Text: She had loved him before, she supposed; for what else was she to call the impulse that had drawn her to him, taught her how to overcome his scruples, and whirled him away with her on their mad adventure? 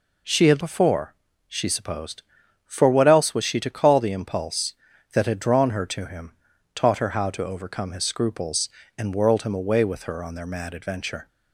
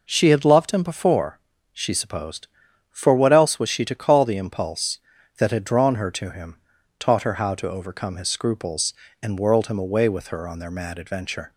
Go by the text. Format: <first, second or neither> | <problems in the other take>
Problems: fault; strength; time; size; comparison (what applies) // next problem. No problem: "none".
second | skips "loved him"; at 0.6 s